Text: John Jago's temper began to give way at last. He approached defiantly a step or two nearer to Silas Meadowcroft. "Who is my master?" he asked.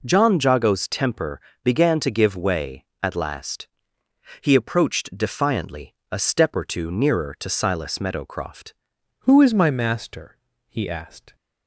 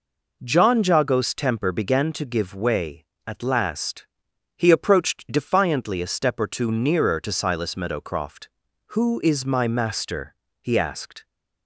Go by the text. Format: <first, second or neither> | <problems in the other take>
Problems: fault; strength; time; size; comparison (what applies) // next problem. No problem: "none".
second | pauses between "temper" and "began"; slight; at 1.3 s; 0.24 s long // pauses between "defiantly" and "a"; slight; at 5.9 s; 0.18 s long // changes voice at "Who"; from 9.1 s on; 2.2 s long